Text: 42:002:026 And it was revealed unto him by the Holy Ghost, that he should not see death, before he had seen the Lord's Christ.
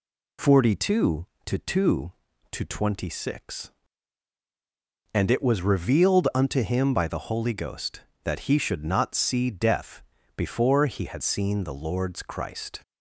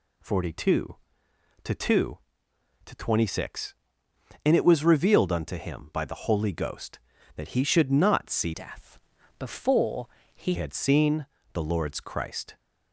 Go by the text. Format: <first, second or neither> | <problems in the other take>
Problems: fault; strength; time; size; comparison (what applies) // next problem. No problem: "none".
first | changes voice from "death" to "he"; from 8.5 to 10.5 s; 2.0 s long // pauses between "before" and "he"; slight; at 10.0 s; 0.28 s long // pauses between "seen" and "the"; slight; at 11.2 s; 0.26 s long